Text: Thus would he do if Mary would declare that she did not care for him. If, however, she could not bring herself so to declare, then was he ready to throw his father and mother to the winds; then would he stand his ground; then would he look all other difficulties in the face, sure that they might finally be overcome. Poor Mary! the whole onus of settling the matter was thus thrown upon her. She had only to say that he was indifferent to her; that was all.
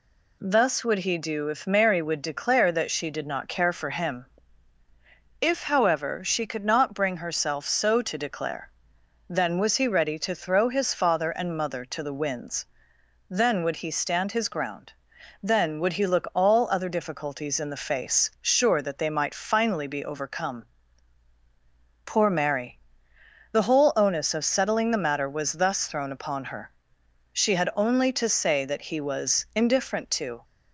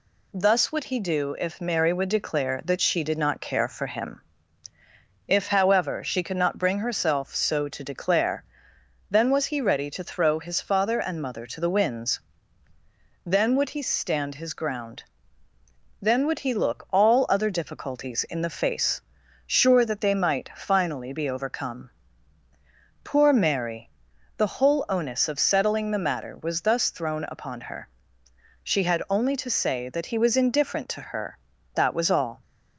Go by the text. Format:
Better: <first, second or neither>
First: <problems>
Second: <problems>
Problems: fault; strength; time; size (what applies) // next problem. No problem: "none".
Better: second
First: stops before "her that was all"; at 30.4 s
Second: none